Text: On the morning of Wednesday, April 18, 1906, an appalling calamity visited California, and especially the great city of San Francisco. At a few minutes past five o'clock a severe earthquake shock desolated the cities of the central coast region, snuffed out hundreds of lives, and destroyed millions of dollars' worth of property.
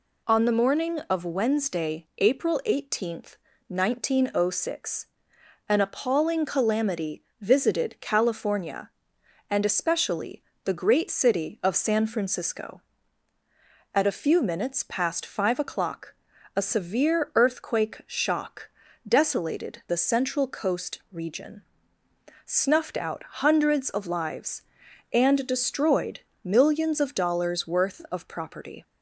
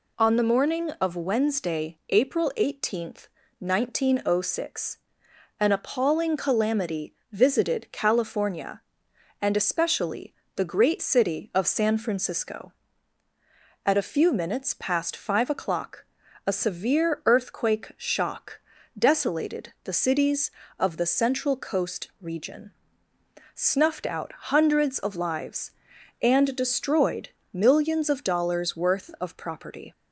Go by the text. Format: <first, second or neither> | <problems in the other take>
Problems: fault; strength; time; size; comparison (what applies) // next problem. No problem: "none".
second | pauses between "calamity" and "visited"; slight; at 7.2 s; 0.18 s long; slight in the second // pauses between "especially" and "the"; slight; at 10.4 s; 0.22 s long; slight in the second // pauses between "o'clock" and "a"; at 16.1 s; 0.42 s long; also in the second // pauses between "shock" and "desolated"; slight; at 18.6 s; 0.36 s long; slight in the second // skips "the cities of"; at 19.8 s // pauses between "destroyed" and "millions"; slight; at 26.2 s; 0.22 s long; slight in the second